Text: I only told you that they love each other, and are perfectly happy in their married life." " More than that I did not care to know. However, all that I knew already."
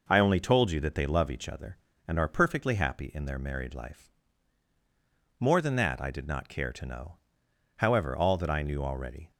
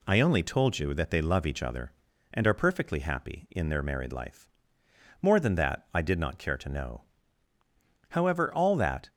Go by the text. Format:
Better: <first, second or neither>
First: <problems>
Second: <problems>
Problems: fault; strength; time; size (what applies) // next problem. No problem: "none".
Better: first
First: none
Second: stops before "I knew already"; at 9.0 s